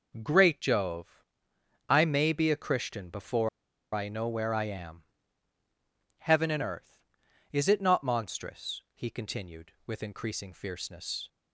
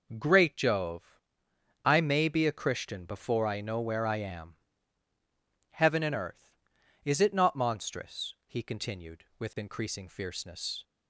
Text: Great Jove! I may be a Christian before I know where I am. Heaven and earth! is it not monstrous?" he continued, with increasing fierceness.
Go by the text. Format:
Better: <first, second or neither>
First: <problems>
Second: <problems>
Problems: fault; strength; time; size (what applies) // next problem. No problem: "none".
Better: second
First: pauses between "before" and "I"; at 3.4 s; 0.43 s long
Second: none